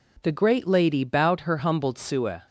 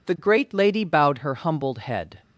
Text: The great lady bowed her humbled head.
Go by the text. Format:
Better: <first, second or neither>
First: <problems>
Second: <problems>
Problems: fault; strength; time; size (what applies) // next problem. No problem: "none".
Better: second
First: says "sueh" for "head"; at 1.9 s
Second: none